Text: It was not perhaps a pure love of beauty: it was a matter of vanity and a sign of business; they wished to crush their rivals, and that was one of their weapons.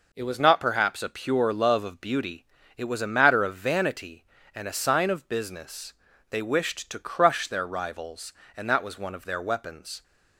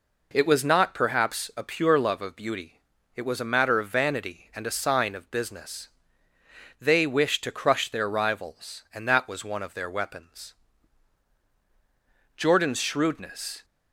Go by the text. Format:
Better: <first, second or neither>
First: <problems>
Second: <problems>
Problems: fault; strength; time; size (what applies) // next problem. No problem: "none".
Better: first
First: none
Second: goes on to say "Jordan's shrewdness"; noticeable; from 12.3 s on; 1.2 s long